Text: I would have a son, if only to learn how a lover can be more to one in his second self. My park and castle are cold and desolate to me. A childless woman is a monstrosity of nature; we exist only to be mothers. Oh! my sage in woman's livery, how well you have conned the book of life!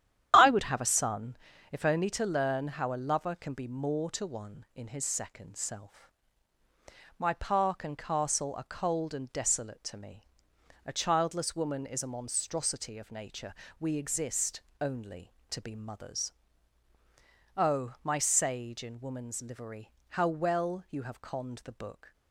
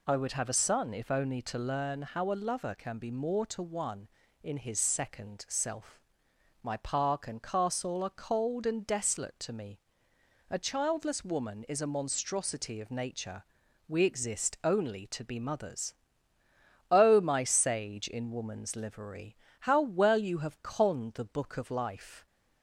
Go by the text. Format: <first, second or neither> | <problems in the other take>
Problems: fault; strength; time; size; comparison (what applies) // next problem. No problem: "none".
second | starts louder than the rest; strong; until 1.3 s; 10.5 dB // pauses between "exist" and "only"; slight; at 14.5 s; 0.22 s long // stops before "of life"; at 22.1 s